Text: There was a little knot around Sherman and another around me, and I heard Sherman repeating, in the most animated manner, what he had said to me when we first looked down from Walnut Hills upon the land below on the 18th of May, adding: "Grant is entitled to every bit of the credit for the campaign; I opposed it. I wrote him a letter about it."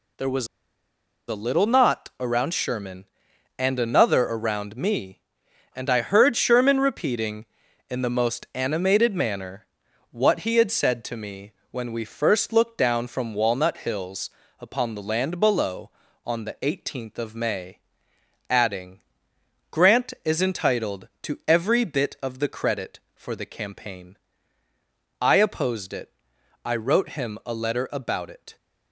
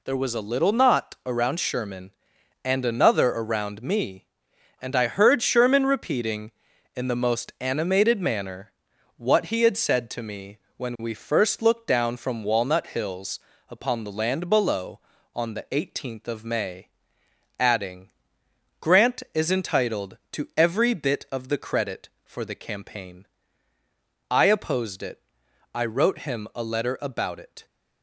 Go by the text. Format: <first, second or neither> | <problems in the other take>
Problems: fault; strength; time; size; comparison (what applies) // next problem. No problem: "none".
second | pauses between "was" and "a"; noticeable; at 0.4 s; 0.81 s long // pauses between "me" and "when"; slight; at 11.5 s; 0.18 s long; slight in the second // pauses between "Hills" and "upon"; slight; at 14.2 s; 0.28 s long; slight in the second